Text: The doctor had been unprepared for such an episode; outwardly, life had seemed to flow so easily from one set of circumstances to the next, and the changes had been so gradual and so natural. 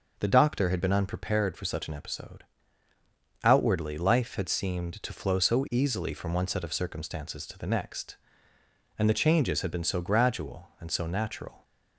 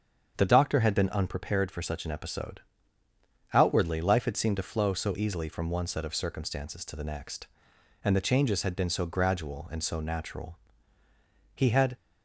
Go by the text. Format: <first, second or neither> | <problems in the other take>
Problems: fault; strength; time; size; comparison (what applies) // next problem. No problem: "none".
first | starts louder than the rest; strong; until 1.3 s; 7.5 dB // goes on to say "He had"; slight; from 11.5 s on; 0.42 s long